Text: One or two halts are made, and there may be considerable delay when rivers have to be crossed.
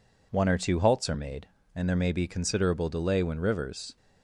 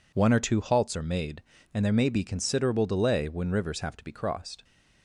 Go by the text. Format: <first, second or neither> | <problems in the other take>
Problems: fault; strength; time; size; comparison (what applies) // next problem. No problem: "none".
second | stops before "have to be crossed"; at 3.9 s